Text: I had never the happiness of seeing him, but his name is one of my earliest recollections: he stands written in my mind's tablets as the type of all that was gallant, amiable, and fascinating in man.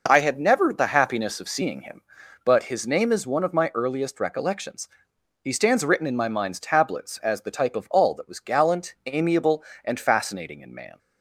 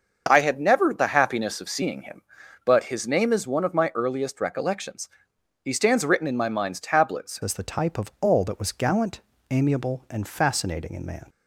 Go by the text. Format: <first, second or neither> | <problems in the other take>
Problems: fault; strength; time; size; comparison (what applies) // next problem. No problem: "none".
first | starts louder than the rest; until 1.2 s; 6.5 dB // changes voice at "as"; from 7.4 s on; 3.8 s long